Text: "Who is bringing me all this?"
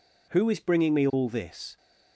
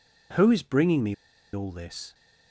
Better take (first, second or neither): first